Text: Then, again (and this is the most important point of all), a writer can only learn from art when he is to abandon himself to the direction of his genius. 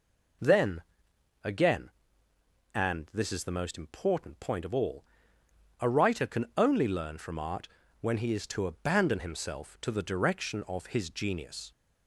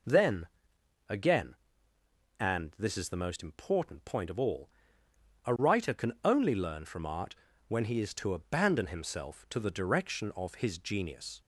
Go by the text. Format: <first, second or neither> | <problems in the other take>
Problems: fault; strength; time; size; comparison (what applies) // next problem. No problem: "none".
neither | pauses between "art" and "when"; slight; the same in both